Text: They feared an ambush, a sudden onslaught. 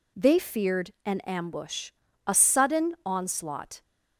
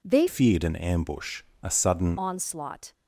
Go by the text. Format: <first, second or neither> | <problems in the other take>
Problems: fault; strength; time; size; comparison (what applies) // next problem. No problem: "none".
first | changes voice from "feared" to "sudden"; from 0.2 to 2.1 s; 1.9 s long